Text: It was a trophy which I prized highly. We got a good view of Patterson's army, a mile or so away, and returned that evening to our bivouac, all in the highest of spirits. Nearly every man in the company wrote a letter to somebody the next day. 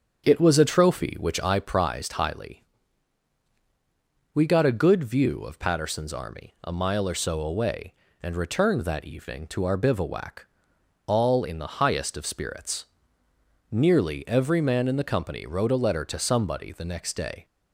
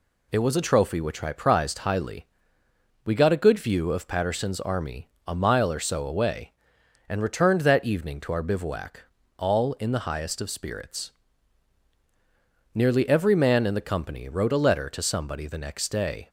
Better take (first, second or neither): second